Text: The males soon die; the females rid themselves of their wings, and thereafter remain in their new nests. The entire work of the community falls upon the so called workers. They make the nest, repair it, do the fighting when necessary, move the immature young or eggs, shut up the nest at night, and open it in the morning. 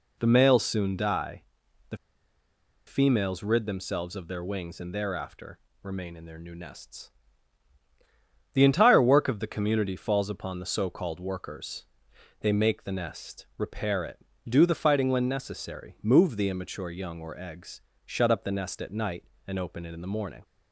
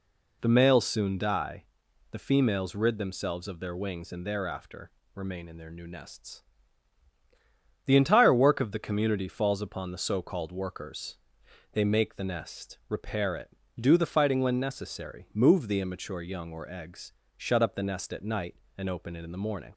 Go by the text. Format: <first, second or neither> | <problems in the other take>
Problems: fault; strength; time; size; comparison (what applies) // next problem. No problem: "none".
second | pauses between "the" and "females"; noticeable; at 1.9 s; 0.90 s long // pauses between "thereafter" and "remain"; slight; at 5.5 s; 0.24 s long; slight in the second